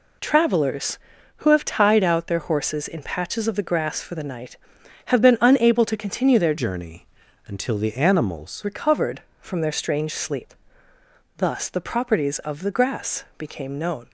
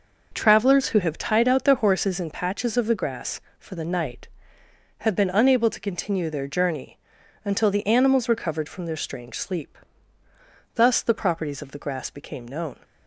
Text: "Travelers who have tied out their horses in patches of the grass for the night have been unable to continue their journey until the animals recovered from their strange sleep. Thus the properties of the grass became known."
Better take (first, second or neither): second